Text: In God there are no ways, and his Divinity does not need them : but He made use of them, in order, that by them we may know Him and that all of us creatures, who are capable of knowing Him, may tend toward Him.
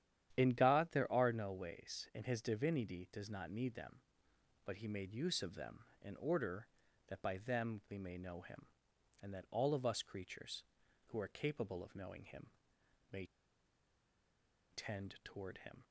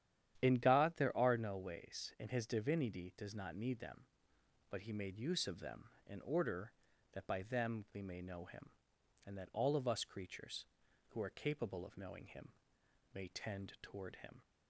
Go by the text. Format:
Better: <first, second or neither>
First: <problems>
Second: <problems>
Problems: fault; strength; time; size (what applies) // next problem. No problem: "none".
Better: second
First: starts louder than the rest; strong; until 1.4 s; 10 dB // pauses between "may" and "tend"; strong; at 13.2 s; 1.4 s long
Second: starts louder than the rest; strong; until 1.4 s; 10 dB